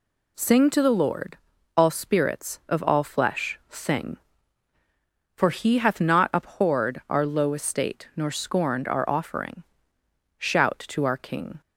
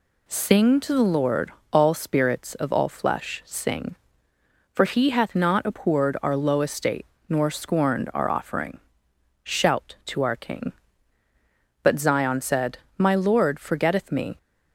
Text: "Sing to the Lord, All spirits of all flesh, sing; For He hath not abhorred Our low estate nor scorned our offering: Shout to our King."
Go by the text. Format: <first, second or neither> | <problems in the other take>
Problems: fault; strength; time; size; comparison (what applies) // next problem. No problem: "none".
first | pauses between "estate" and "nor"; slight; at 7.0 s; 0.24 s long // goes on to say "But Zion said My Lord forgetteth me"; strong; from 11.8 s on; 2.5 s long